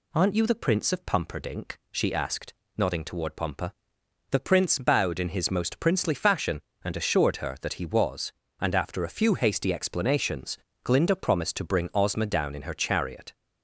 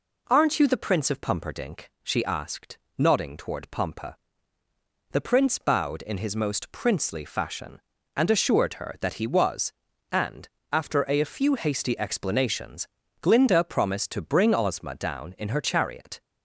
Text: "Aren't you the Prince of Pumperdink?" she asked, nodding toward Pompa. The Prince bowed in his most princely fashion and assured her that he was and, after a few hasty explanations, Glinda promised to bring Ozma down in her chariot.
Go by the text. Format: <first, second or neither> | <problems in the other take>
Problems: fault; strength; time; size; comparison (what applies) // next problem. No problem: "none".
first | says "a" twice; at 11.2 s